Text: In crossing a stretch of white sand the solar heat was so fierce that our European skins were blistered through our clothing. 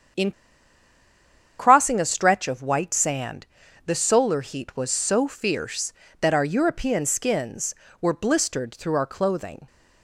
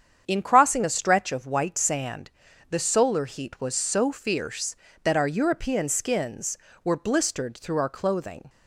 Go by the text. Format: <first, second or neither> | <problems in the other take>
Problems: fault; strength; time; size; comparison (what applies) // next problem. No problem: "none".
second | starts louder than the rest; strong; until 2.4 s; 8 dB; strong in the second // pauses between "In" and "crossing"; strong; at 0.3 s; 1.2 s long // pauses between "sand" and "the"; at 3.4 s; 0.40 s long; also in the second